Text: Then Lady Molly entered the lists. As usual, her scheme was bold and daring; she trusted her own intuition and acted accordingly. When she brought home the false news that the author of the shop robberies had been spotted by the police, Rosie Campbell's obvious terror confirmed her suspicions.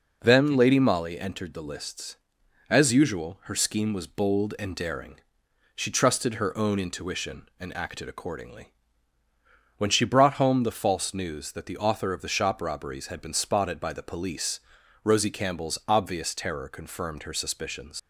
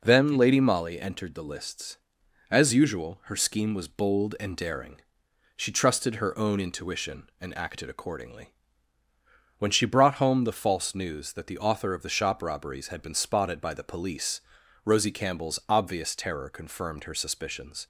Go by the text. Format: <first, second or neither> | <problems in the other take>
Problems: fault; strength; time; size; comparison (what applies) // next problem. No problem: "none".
second | leaves "suspicions" unfinished; at 17.9 s; 60 ms